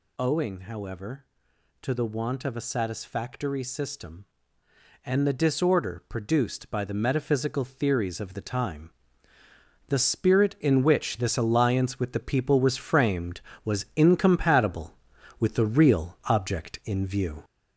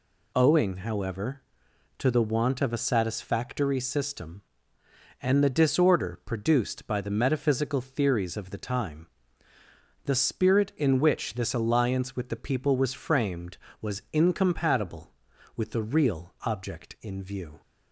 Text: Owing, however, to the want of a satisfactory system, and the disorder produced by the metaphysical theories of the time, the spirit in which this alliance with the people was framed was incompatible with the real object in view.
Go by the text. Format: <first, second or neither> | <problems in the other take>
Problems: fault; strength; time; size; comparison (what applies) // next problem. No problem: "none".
second | gets louder; noticeable; throughout; 4 dB